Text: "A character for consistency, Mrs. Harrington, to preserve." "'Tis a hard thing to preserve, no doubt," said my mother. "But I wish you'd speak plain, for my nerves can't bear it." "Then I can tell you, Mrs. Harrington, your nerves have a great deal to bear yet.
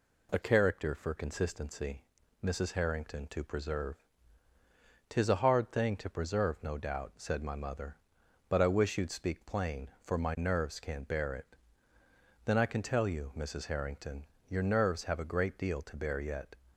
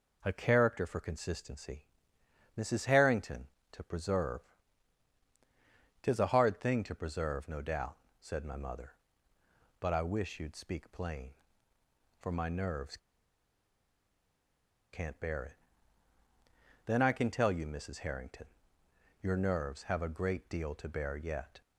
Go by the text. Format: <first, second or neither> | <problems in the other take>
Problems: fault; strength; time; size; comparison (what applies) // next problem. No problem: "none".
first | pauses between "nerves" and "can't"; strong; at 12.9 s; 1.9 s long